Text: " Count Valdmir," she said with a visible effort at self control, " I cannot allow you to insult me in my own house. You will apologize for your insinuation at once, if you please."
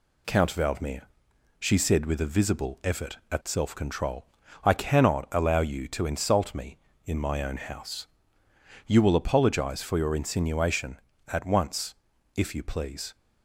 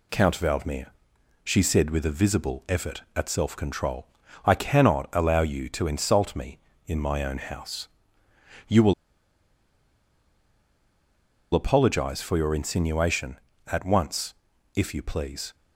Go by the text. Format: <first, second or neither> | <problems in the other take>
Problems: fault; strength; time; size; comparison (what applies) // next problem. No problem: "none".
first | pauses between "will" and "apologize"; strong; at 8.9 s; 2.6 s long